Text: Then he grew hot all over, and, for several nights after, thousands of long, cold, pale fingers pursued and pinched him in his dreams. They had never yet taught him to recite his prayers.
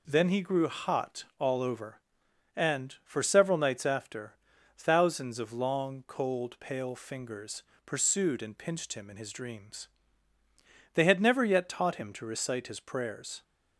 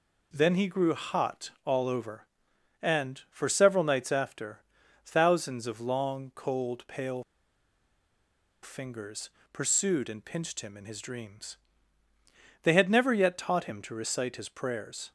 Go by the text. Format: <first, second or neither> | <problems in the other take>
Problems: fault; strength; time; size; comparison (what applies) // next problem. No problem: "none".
first | pauses between "pale" and "fingers"; strong; at 7.2 s; 1.4 s long // pauses between "fingers" and "pursued"; slight; at 9.2 s; 0.24 s long; slight in the first